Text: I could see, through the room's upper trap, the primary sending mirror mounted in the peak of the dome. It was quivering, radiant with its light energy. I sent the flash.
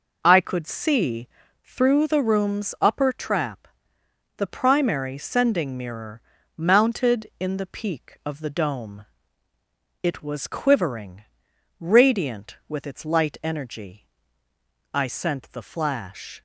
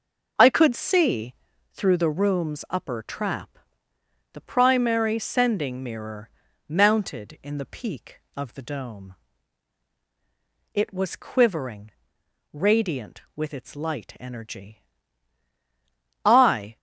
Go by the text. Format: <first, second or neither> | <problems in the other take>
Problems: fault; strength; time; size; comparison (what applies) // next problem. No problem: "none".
first | pauses between "mirror" and "mounted"; at 6.2 s; 0.38 s long; also in the first // stops before "sent the flash"; at 16.7 s